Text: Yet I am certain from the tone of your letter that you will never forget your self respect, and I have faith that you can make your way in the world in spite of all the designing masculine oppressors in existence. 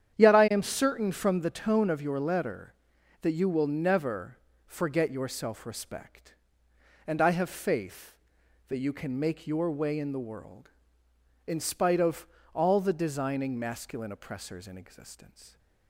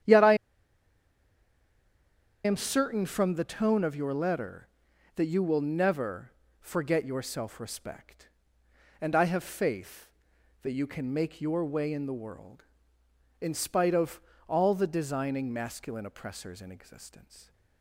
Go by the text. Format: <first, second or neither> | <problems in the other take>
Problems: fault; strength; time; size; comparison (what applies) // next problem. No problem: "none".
first | starts louder than the rest; strong; until 3.1 s; 9.5 dB; strong in the first // pauses between "I" and "am"; strong; at 0.3 s; 2.1 s long // pauses between "never" and "forget"; slight; at 6.3 s; 0.28 s long; slight in the first // pauses between "of" and "all"; slight; at 14.1 s; 0.28 s long; slight in the first